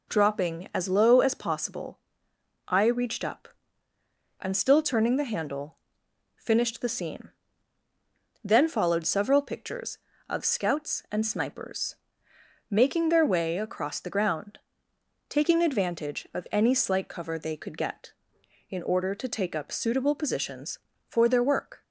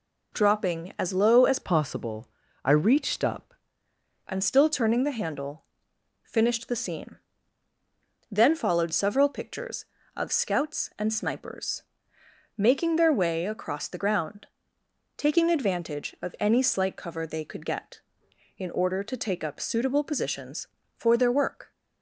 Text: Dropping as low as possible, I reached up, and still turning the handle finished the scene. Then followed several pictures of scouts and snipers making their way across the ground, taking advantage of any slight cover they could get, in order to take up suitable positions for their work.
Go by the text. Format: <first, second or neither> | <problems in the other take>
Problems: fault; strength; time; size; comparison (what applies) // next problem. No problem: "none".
first | changes voice from "possible" to "up"; from 1.6 to 3.5 s; 1.9 s long // pauses between "handle" and "finished"; noticeable; at 5.6 s; 0.58 s long; noticeable in the first // pauses between "snipers" and "making"; noticeable; at 11.8 s; 0.74 s long; noticeable in the first